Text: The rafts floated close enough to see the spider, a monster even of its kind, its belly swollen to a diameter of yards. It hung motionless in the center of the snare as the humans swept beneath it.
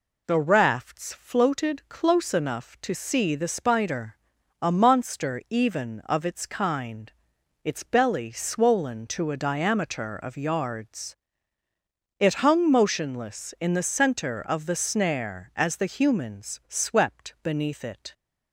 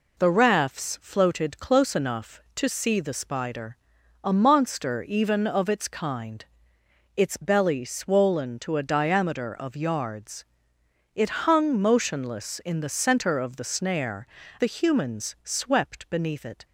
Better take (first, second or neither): first